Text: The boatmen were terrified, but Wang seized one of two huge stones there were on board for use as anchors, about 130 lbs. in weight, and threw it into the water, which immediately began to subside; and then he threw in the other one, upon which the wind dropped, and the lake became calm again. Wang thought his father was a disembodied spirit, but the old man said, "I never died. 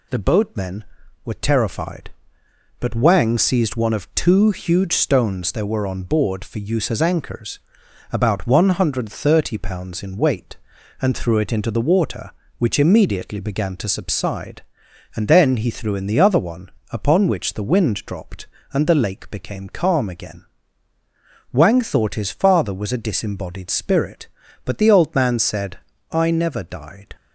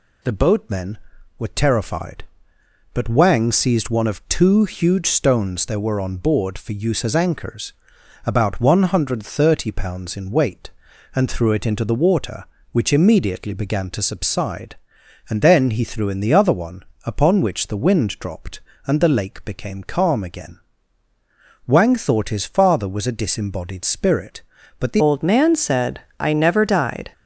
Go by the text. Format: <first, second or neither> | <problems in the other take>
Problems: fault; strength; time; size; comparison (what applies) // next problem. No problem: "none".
first | changes voice at "old"; from 24.9 s on; 2.2 s long